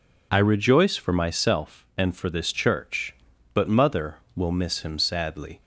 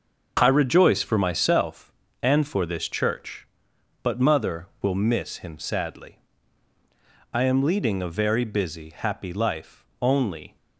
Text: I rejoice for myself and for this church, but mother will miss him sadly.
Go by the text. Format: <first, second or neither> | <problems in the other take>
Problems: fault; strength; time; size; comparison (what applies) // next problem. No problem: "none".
first | starts louder than the rest; noticeable; until 1.4 s; 6 dB // goes on to say "I am leading a very busy happy life only"; strong; from 7.3 s on; 3.2 s long